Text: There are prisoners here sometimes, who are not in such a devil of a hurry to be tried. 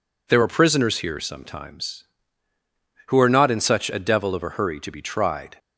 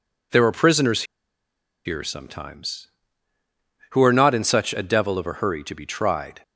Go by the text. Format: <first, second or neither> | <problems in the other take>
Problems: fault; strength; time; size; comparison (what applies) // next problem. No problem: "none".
first | pauses between "prisoners" and "here"; noticeable; at 1.0 s; 0.82 s long